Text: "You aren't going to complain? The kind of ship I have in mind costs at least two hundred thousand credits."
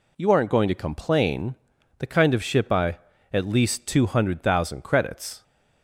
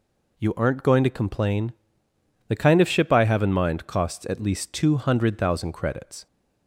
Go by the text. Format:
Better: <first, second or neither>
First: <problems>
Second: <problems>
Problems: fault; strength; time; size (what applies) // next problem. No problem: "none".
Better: second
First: skips "have in mind costs"; at 3.1 s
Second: none